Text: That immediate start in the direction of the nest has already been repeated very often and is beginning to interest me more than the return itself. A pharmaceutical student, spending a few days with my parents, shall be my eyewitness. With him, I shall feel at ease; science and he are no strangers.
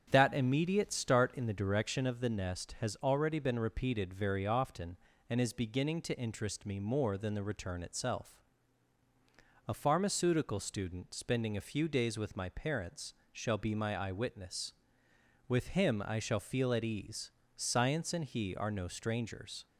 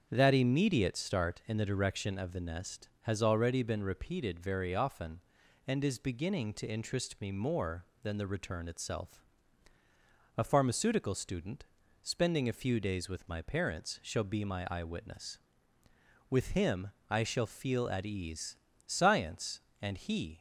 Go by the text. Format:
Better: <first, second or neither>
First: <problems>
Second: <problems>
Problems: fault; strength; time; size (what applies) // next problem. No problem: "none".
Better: first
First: starts louder than the rest; strong; until 1.1 s; 8 dB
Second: starts louder than the rest; strong; until 1.1 s; 7.5 dB // stops before "are no strangers"; at 20.3 s